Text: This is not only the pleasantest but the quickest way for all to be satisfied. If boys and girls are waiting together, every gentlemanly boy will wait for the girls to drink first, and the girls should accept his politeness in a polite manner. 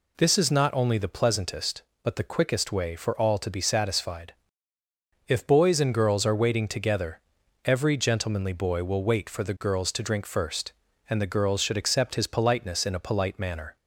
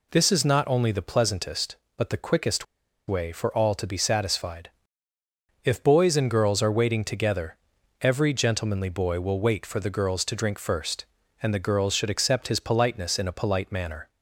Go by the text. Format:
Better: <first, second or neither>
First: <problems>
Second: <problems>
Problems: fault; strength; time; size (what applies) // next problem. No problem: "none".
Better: first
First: none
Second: pauses between "quickest" and "way"; at 2.6 s; 0.43 s long